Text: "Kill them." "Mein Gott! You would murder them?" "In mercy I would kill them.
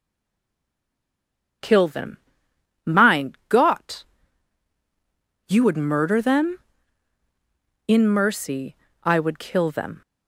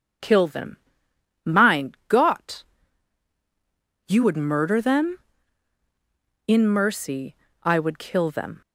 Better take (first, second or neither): second